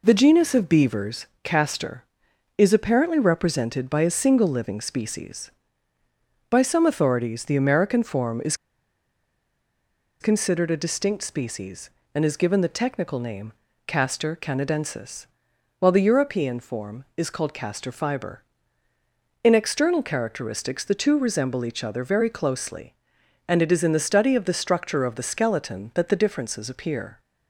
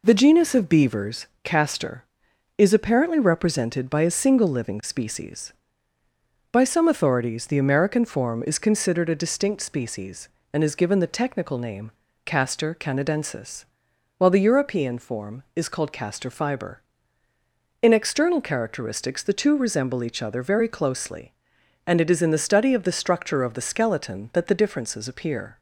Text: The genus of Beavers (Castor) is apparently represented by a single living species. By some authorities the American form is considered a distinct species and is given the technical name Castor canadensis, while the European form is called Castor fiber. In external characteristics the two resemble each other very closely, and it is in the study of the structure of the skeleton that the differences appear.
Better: second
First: pauses between "is" and "considered"; strong; at 8.5 s; 1.6 s long // pauses between "name" and "Castor"; slight; at 13.5 s; 0.34 s long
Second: pauses between "name" and "Castor"; slight; at 11.9 s; 0.34 s long

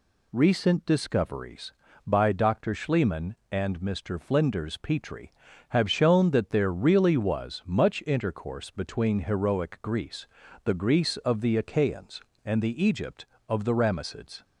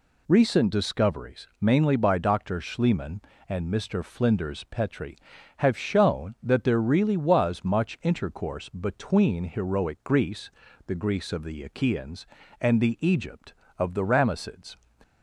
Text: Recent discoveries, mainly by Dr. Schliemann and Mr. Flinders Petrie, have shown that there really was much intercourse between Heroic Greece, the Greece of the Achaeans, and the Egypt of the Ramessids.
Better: second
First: skips "mainly"; at 1.8 s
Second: none

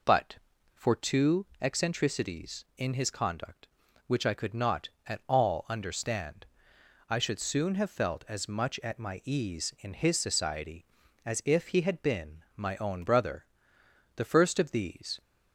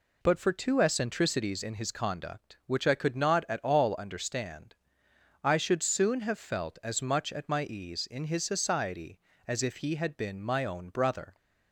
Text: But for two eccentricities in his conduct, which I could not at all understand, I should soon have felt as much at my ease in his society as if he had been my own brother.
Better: second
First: goes on to say "The first of these"; noticeable; from 14.1 s on; 1.0 s long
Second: none

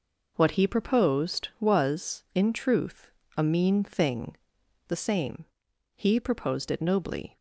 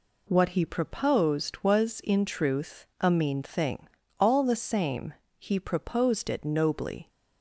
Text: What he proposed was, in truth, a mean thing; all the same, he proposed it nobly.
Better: second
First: skips "all"; at 4.6 s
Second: none

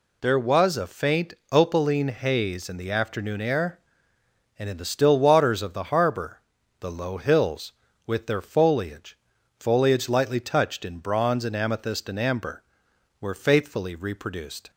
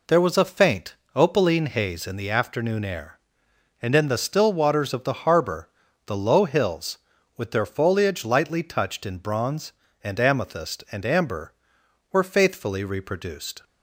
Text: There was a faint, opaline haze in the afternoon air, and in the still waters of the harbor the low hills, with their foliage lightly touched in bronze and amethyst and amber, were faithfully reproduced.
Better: second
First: pauses between "harbor" and "the"; at 6.4 s; 0.40 s long // says "foliage" twice; at 9.6 s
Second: pauses between "harbor" and "the"; slight; at 5.6 s; 0.36 s long

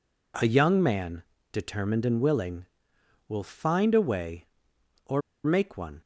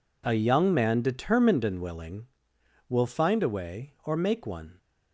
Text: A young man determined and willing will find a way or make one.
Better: second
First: pauses between "man" and "determined"; slight; at 1.2 s; 0.30 s long // pauses between "or" and "make"; slight; at 5.2 s; 0.23 s long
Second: none

